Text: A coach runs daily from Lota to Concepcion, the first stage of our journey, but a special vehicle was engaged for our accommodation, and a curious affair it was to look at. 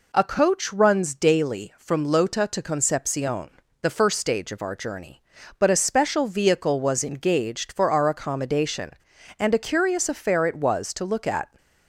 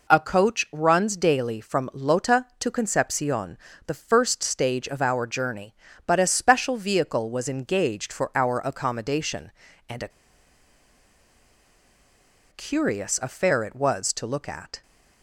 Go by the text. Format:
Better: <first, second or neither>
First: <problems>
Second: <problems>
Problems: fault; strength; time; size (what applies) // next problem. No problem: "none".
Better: first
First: none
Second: pauses between "a" and "curious"; strong; at 10.0 s; 2.4 s long